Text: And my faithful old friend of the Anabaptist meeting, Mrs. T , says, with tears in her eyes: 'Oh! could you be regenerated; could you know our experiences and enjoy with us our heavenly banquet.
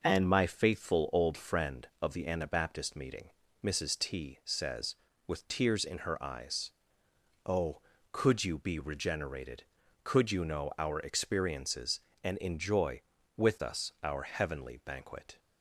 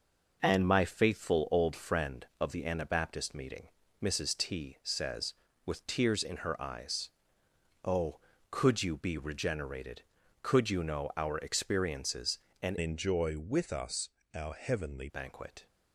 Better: first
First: none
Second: changes voice from "enjoy" to "heavenly"; from 12.7 to 15.0 s; 2.3 s long // pauses between "us" and "our"; slight; at 14.0 s; 0.24 s long

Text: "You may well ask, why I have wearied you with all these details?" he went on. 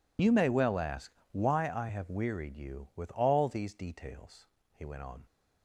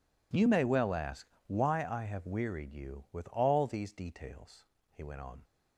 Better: second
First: loses the start of "You"; at 0.1 s; 40 ms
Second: none

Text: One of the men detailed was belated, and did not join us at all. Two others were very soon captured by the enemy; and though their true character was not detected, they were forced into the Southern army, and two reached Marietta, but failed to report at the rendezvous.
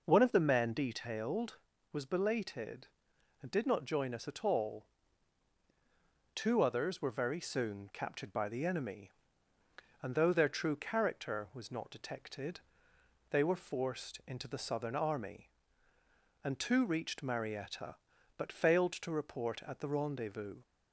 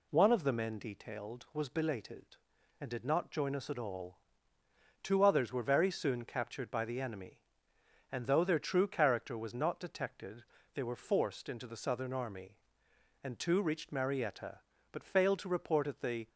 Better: first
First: none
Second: stops before "rendezvous"; at 16.2 s

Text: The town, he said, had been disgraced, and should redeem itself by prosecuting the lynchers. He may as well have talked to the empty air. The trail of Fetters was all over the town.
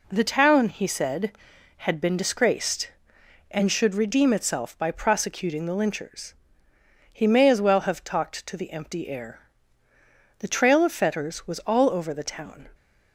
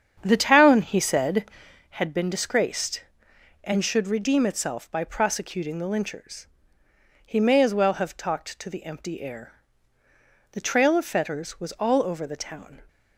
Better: first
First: none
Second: starts louder than the rest; strong; until 1.8 s; 8 dB

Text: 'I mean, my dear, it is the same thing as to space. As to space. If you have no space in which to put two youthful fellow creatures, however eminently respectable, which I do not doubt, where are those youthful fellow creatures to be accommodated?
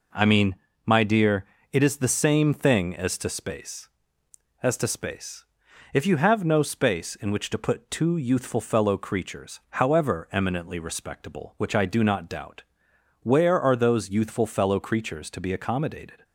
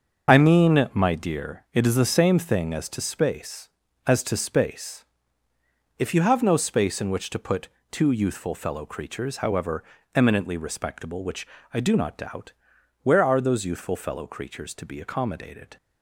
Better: first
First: none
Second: loses the start of "I"; at 0.2 s; 25 ms // starts louder than the rest; until 1.3 s; 6.5 dB // pauses between "put" and "two"; slight; at 7.6 s; 0.24 s long // pauses between "however" and "eminently"; slight; at 9.8 s; 0.32 s long // pauses between "which" and "I"; slight; at 11.4 s; 0.26 s long

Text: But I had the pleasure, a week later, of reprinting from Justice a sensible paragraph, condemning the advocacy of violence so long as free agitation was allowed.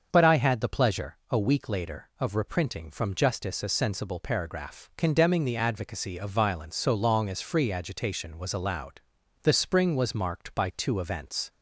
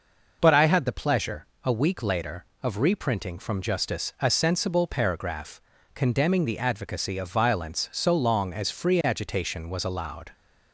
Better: second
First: starts louder than the rest; until 1.1 s; 6.5 dB // goes on to say "The spring was marked by two events"; strong; from 9.4 s on; 2.0 s long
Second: none

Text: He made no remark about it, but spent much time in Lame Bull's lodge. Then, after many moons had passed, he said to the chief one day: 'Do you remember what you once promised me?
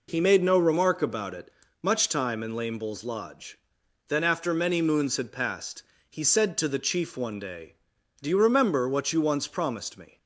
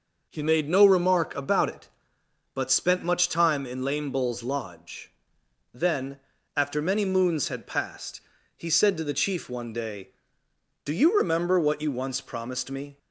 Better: second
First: skips "but spent"; at 1.6 s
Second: none

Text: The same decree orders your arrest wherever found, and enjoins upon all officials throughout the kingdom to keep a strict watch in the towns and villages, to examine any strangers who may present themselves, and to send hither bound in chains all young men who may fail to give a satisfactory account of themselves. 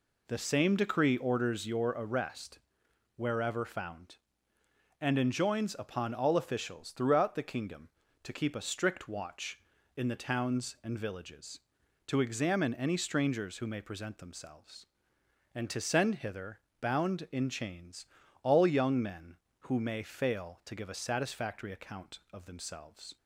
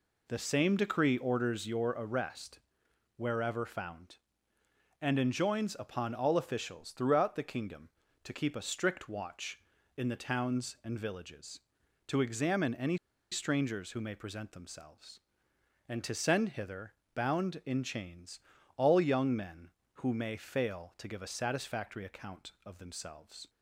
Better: first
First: pauses between "arrest" and "wherever"; noticeable; at 2.5 s; 0.58 s long // pauses between "hither" and "bound"; slight; at 16.5 s; 0.22 s long // pauses between "chains" and "all"; slight; at 18.0 s; 0.36 s long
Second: pauses between "arrest" and "wherever"; noticeable; at 2.5 s; 0.58 s long // pauses between "any" and "strangers"; slight; at 12.9 s; 0.35 s long // pauses between "hither" and "bound"; slight; at 16.9 s; 0.22 s long // pauses between "chains" and "all"; slight; at 18.3 s; 0.36 s long

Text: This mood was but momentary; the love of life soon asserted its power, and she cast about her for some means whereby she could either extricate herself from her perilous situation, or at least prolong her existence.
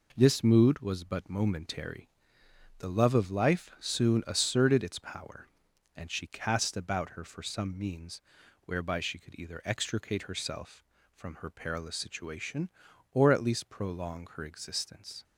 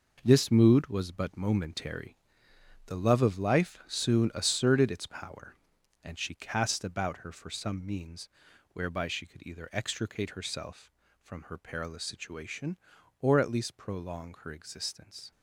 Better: first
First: pauses between "means" and "whereby"; noticeable; at 8.1 s; 0.46 s long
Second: gets quieter; strong; throughout; 9 dB // pauses between "means" and "whereby"; noticeable; at 8.2 s; 0.46 s long

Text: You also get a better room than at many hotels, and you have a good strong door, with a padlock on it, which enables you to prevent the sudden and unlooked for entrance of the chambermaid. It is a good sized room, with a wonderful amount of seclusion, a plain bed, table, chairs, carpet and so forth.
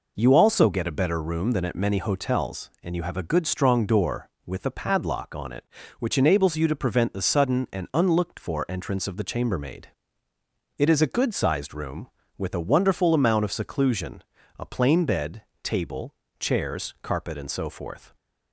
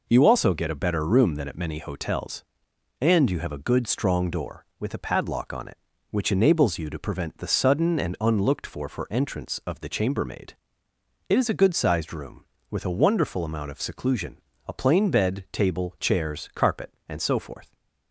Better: first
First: none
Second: says "for" twice; at 8.8 s

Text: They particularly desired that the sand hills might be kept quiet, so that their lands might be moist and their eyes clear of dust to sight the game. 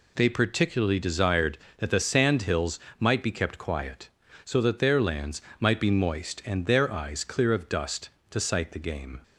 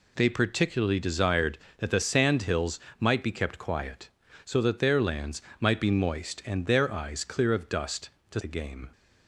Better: first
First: pauses between "hills" and "might"; slight; at 2.7 s; 0.22 s long // pauses between "lands" and "might"; slight; at 5.4 s; 0.16 s long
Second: pauses between "hills" and "might"; slight; at 2.7 s; 0.22 s long // pauses between "lands" and "might"; slight; at 5.4 s; 0.16 s long // skips "sight"; at 8.4 s

